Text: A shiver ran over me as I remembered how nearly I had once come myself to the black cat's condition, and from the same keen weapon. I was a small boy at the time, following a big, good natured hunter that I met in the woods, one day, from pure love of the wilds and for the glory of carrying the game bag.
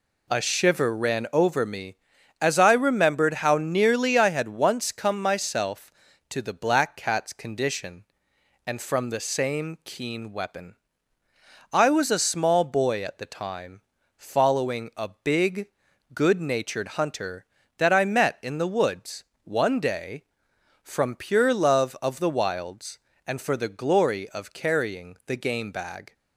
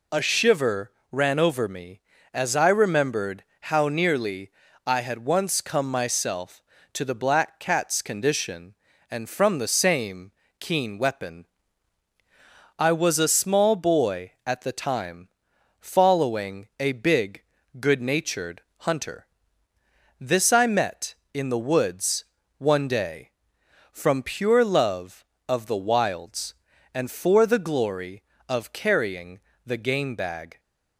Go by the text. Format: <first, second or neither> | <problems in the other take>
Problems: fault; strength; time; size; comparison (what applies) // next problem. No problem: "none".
first | pauses between "shiver" and "ran"; slight; at 0.9 s; 0.20 s long // pauses between "remembered" and "how"; slight; at 3.4 s; 0.18 s long // pauses between "nearly" and "I"; slight; at 4.4 s; 0.34 s long // pauses between "same" and "keen"; slight; at 10.3 s; 0.26 s long // pauses between "natured" and "hunter"; slight; at 18.6 s; 0.18 s long // says "this" for "that"; at 20.2 s // pauses between "carrying" and "the"; slight; at 29.3 s; 0.26 s long